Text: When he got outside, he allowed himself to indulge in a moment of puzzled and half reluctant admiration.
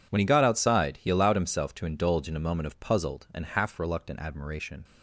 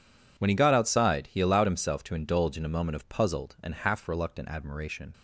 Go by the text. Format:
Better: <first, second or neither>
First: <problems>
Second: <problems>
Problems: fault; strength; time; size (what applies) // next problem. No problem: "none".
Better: neither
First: none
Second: none